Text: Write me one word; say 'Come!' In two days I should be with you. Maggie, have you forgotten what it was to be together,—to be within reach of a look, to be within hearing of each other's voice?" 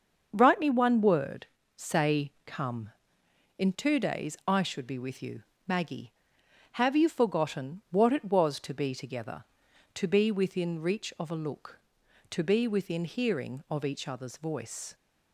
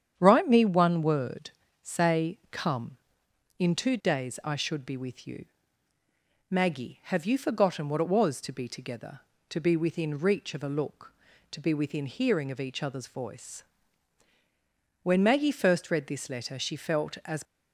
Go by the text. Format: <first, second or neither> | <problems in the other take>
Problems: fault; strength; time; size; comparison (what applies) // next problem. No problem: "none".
first | starts louder than the rest; strong; until 1.1 s; 9 dB; also in the first // goes on to say "When Maggie first read this letter she felt as"; strong; from 15.0 s on; 2.4 s long